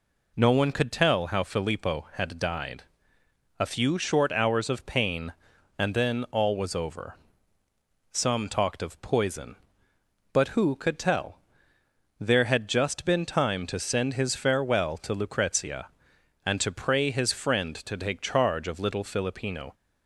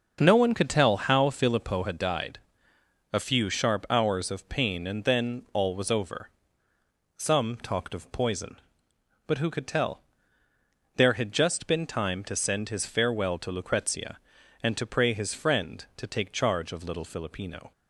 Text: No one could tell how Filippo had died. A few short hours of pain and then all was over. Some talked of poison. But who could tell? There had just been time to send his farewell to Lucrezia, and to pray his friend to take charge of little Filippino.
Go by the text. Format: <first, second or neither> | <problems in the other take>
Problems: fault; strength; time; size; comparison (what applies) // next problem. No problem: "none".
first | starts louder than the rest; until 1.2 s; 6 dB // says "sharp" for "short"; at 3.4 s